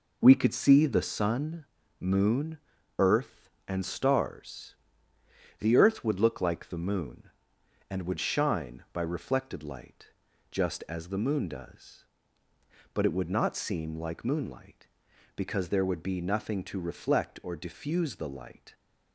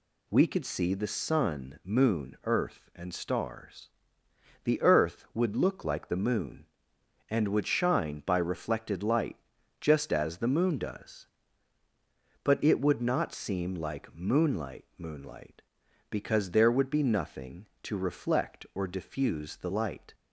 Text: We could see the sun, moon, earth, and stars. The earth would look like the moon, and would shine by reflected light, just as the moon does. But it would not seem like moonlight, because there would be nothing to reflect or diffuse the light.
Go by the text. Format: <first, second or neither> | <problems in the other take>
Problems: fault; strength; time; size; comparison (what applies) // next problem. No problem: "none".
first | says "moonlight" twice; at 14.9 s